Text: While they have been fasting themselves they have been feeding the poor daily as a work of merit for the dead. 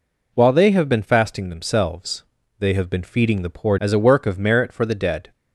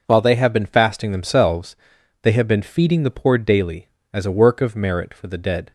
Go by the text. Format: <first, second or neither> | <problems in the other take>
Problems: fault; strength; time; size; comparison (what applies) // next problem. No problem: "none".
second | pauses between "themselves" and "they"; slight; at 2.2 s; 0.36 s long; noticeable in the second // skips "daily"; at 3.7 s